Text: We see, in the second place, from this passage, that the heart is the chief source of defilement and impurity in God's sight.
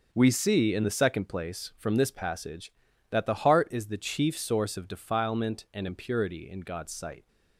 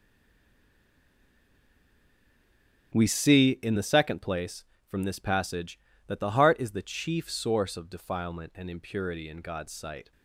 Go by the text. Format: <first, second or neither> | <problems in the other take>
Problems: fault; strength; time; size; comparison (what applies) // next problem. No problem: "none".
first | stays silent before the first word; strong; until 2.9 s; 2.9 s long // starts louder than the rest; strong; until 3.9 s; 8.5 dB